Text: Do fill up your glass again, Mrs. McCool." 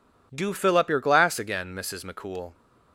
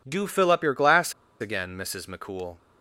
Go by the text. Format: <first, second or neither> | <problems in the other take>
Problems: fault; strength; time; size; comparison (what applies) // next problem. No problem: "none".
first | pauses between "glass" and "again"; slight; at 1.1 s; 0.28 s long